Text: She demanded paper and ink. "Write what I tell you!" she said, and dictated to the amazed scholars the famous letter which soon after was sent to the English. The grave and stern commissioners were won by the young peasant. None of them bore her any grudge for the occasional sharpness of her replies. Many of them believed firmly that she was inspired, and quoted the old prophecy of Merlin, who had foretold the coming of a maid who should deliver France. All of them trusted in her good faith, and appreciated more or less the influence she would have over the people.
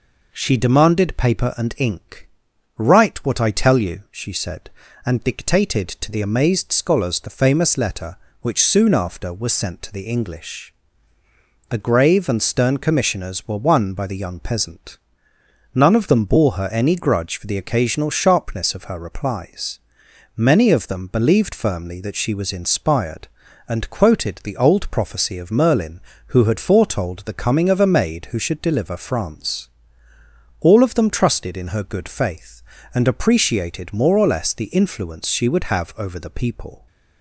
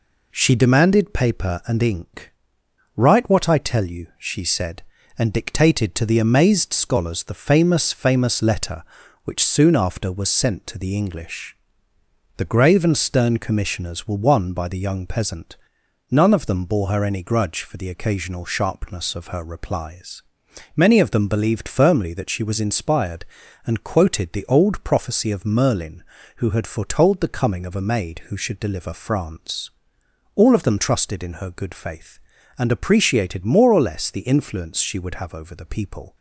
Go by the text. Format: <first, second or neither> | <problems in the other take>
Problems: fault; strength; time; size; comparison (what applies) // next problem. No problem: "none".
first | says "famous" twice; at 7.9 s